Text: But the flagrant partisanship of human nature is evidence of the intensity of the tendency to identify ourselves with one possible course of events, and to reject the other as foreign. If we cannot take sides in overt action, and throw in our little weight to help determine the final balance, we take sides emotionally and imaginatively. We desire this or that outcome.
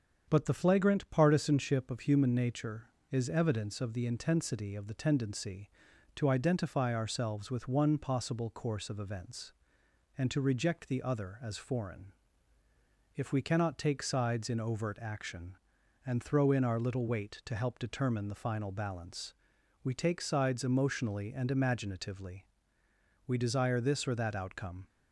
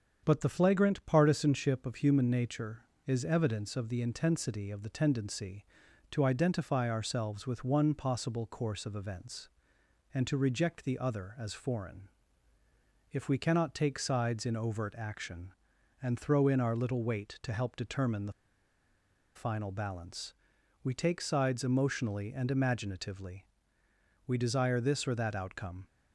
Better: first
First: starts louder than the rest; strong; until 1.2 s; 7.5 dB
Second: starts louder than the rest; strong; until 1.2 s; 7.5 dB // pauses between "the" and "final"; at 18.3 s; 1.0 s long

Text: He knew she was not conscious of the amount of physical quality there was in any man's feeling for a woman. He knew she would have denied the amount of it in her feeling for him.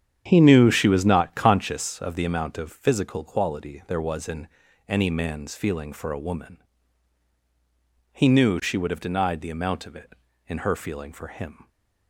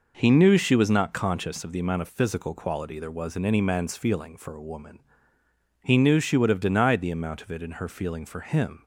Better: second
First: starts louder than the rest; strong; until 1.7 s; 9 dB // pauses between "in" and "any"; at 4.4 s; 0.40 s long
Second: none

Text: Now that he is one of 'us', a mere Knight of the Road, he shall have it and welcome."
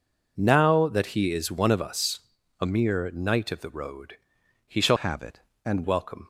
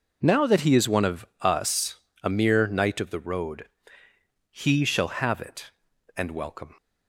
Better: second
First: changes voice from "have" to "and"; from 4.9 to 5.8 s; 0.9 s long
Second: none

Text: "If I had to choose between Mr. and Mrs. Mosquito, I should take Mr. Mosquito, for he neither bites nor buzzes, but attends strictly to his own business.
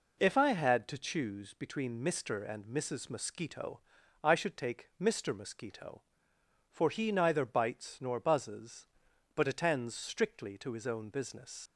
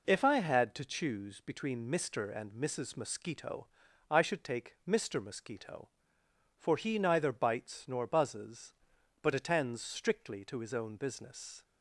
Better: second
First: leaves "business" unfinished; at 11.6 s; 110 ms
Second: none

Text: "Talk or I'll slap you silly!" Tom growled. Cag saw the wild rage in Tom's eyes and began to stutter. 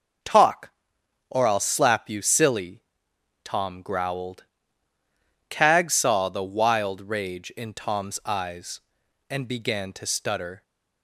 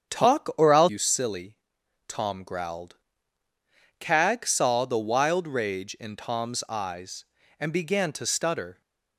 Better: first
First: none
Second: starts louder than the rest; strong; until 1.2 s; 8 dB // skips "slap"; at 0.8 s

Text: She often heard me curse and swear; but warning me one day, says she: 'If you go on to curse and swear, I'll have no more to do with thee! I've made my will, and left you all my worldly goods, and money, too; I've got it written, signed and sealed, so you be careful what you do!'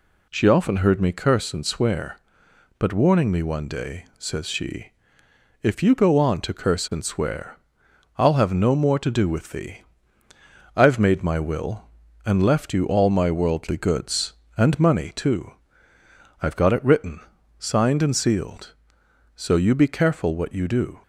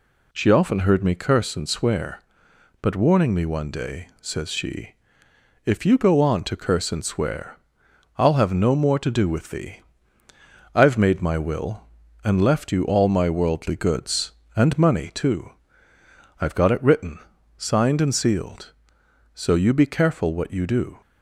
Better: neither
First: none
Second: none

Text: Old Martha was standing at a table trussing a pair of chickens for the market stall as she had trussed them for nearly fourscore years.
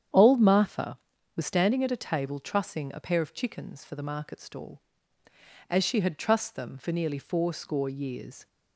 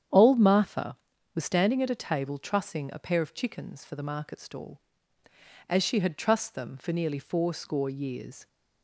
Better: neither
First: starts louder than the rest; strong; until 1.5 s; 9 dB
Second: starts louder than the rest; strong; until 1.4 s; 9 dB

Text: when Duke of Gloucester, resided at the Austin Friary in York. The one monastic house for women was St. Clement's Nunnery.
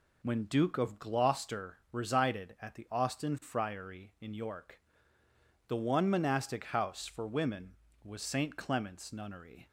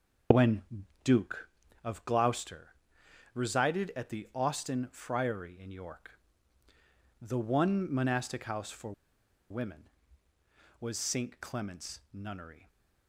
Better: first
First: none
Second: pauses between "when" and "Duke"; at 0.6 s; 0.42 s long // pauses between "for" and "women"; noticeable; at 8.9 s; 0.58 s long // stays silent after the last word; slight; from 12.5 s on; 0.5 s long

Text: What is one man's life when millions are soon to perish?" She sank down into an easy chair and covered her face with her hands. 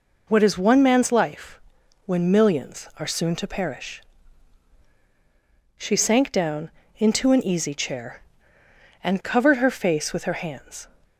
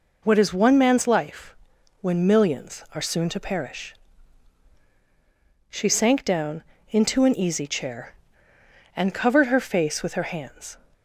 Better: neither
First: pauses between "life" and "when"; noticeable; at 1.5 s; 0.46 s long // pauses between "down" and "into"; slight; at 6.7 s; 0.24 s long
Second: pauses between "life" and "when"; noticeable; at 1.5 s; 0.46 s long // pauses between "down" and "into"; slight; at 6.6 s; 0.24 s long

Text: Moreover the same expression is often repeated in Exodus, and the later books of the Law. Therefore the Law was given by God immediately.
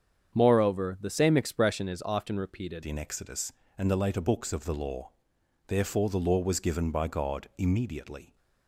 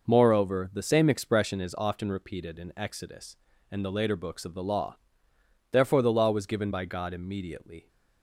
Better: second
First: starts louder than the rest; strong; until 1.3 s; 7.5 dB // changes voice at "in"; from 2.8 s on; 5.5 s long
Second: none

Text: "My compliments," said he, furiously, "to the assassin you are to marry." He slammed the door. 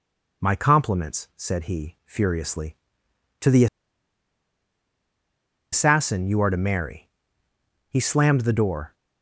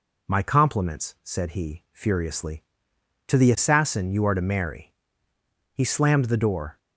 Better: second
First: pauses between "the" and "assassin"; strong; at 3.6 s; 2.0 s long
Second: none

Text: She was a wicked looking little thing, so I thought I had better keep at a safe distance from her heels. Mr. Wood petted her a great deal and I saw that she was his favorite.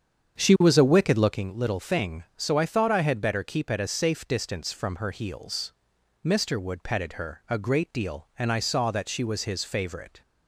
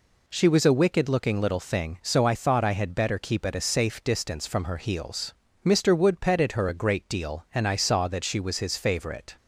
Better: second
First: starts louder than the rest; strong; until 1.5 s; 7.5 dB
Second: none

